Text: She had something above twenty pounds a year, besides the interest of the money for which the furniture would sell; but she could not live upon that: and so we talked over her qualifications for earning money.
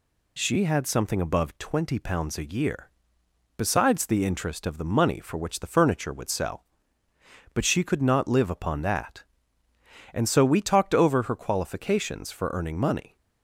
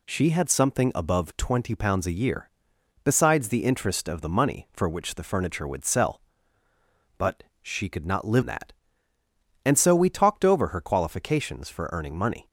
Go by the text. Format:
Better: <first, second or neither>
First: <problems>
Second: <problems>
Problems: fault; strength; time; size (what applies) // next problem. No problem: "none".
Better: first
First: none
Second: pauses between "but" and "she"; slight; at 7.4 s; 0.20 s long // skips "upon"; at 8.4 s